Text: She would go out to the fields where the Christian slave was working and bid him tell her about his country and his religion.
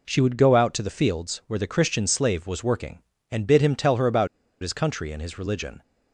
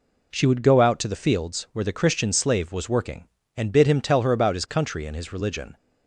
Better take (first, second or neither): second